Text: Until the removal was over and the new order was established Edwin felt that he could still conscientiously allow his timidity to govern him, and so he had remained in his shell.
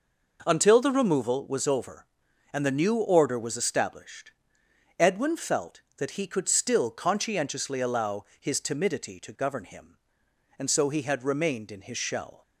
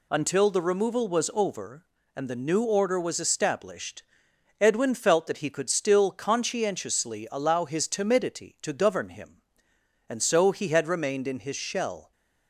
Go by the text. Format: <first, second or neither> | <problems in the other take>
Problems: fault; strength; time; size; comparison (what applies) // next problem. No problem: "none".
neither | pauses between "established" and "Edwin"; noticeable; the same in both